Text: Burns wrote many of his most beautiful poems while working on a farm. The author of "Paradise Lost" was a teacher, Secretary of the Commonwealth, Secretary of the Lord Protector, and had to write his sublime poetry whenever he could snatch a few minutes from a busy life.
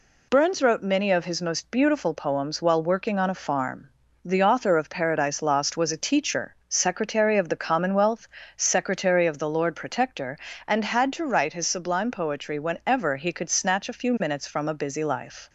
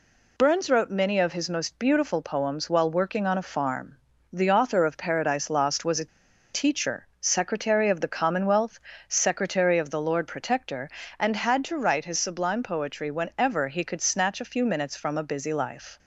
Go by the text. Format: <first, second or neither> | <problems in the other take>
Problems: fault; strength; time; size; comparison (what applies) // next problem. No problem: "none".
first | pauses between "a" and "teacher"; noticeable; at 6.0 s; 0.46 s long